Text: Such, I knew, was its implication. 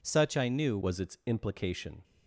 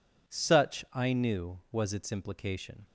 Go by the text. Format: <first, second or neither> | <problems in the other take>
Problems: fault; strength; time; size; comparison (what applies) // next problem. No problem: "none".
second | changes voice at "was"; from 0.8 s on; 1.2 s long